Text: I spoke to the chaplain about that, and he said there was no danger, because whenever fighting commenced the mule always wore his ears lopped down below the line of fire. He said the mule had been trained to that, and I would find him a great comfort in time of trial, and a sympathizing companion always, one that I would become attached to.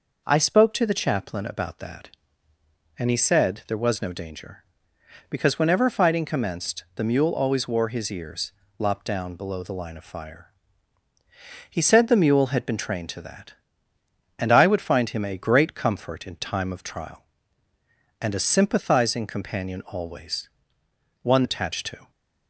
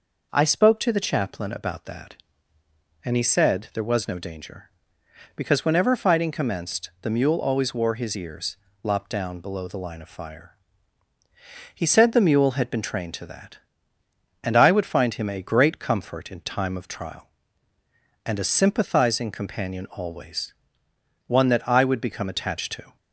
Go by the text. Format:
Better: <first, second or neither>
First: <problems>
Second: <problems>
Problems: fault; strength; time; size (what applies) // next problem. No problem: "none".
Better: second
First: pauses between "ears" and "lopped"; slight; at 8.5 s; 0.26 s long // skips "that I would become"; at 21.4 s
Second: pauses between "ears" and "lopped"; slight; at 8.5 s; 0.26 s long